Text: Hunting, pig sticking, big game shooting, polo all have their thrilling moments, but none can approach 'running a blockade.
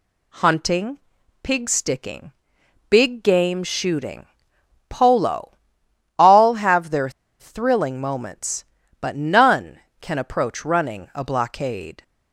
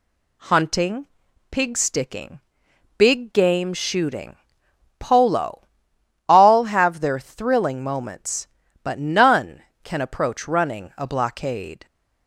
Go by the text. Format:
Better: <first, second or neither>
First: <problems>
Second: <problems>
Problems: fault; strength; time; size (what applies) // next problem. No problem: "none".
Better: second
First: pauses between "polo" and "all"; noticeable; at 5.5 s; 0.68 s long // pauses between "their" and "thrilling"; slight; at 7.0 s; 0.30 s long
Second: pauses between "polo" and "all"; noticeable; at 5.6 s; 0.68 s long